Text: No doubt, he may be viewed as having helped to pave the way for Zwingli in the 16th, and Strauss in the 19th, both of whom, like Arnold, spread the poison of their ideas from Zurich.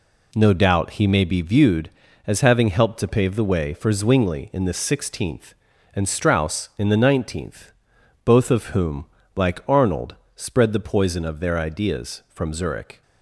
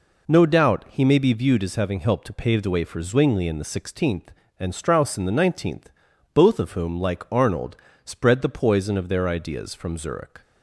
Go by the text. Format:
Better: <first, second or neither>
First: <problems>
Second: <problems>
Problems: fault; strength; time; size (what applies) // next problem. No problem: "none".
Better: neither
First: none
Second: none